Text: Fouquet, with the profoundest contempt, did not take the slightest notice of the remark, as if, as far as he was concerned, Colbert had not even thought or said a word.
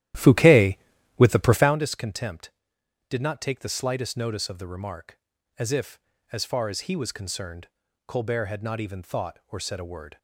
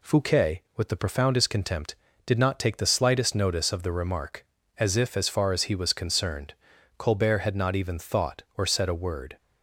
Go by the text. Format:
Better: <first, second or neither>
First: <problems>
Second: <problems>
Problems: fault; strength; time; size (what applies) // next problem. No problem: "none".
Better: second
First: starts louder than the rest; strong; until 1.8 s; 13 dB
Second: none